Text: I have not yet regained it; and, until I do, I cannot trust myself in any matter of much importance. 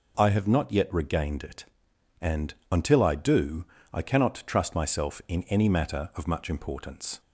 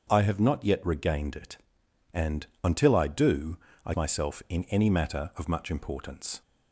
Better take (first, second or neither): first